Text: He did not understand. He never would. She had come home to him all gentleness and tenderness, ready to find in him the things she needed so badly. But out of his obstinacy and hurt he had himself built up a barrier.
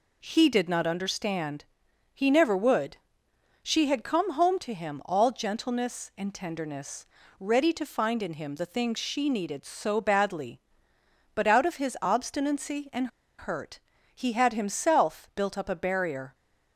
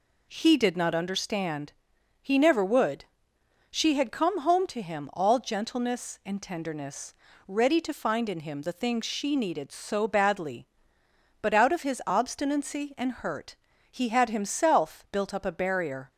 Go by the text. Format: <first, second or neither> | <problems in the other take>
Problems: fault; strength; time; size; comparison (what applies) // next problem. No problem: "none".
second | pauses between "and" and "hurt"; slight; at 13.0 s; 0.30 s long // pauses between "hurt" and "he"; slight; at 13.7 s; 0.34 s long; slight in the second